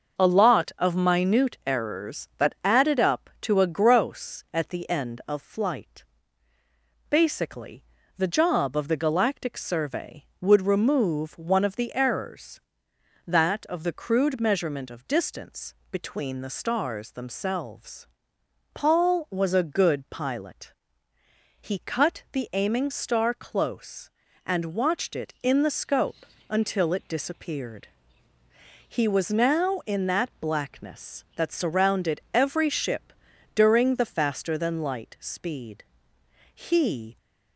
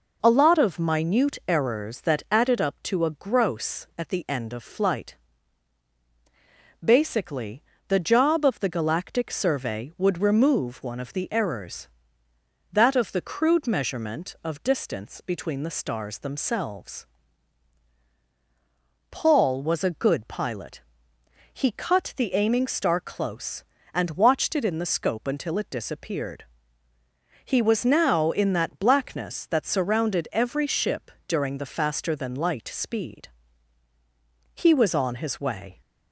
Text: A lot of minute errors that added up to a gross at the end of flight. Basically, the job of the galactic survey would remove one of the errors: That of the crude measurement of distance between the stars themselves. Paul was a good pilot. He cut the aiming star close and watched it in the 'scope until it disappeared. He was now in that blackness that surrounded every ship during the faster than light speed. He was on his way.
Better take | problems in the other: second | starts louder than the rest; until 1.2 s; 6.5 dB // pauses between "distance" and "between"; slight; at 15.7 s; 0.18 s long // pauses between "scope" and "until"; slight; at 26.2 s; 0.24 s long // pauses between "ship" and "during"; at 33.1 s; 0.44 s long; slight in the second // stops before "was on his way"; at 37.1 s

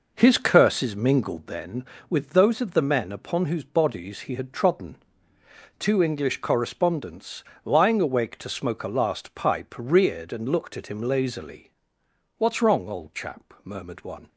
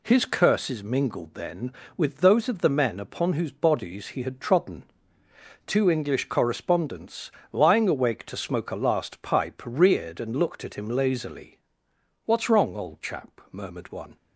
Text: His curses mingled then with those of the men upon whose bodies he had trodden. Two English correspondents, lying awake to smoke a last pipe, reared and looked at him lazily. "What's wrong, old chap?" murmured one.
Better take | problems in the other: second | starts louder than the rest; noticeable; until 1.6 s; 5.5 dB

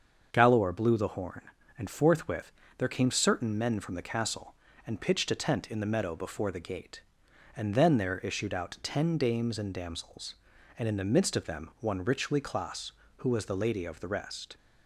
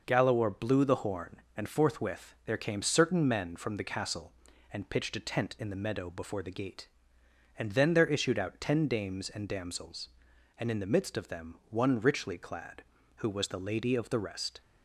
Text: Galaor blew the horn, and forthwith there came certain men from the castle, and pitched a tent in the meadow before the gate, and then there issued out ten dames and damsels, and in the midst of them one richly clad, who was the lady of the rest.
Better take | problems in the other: second | starts louder than the rest; until 1.3 s; 6.5 dB // pauses between "forthwith" and "there"; slight; at 2.5 s; 0.26 s long // says "clas" for "clad"; at 12.4 s

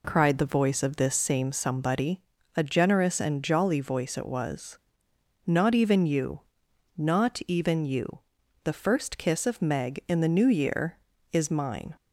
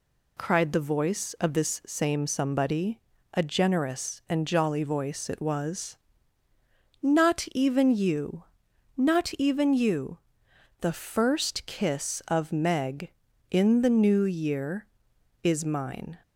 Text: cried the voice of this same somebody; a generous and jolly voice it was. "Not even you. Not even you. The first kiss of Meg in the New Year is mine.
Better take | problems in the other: neither | none

